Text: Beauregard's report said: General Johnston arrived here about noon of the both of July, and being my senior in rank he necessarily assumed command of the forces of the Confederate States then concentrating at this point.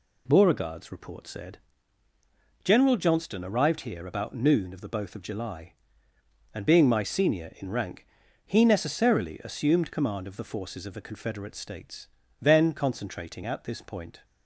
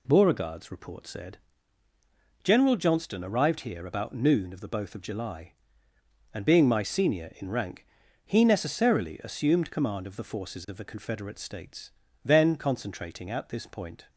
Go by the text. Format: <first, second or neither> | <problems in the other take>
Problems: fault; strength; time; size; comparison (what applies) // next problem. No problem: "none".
neither | pauses between "rank" and "he"; the same in both // pauses between "States" and "then"; slight; the same in both